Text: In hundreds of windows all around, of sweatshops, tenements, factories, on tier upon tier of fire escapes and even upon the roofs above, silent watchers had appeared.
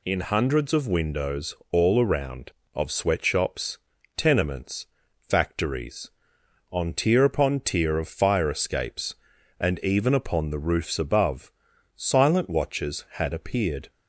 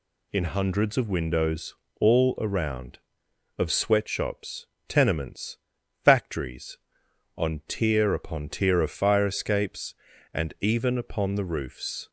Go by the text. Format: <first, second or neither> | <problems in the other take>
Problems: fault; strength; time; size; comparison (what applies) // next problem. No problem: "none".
first | pauses between "windows" and "all"; slight; at 1.7 s; 0.26 s long; slight in the first // stops before "above silent watchers had appeared"; at 12.0 s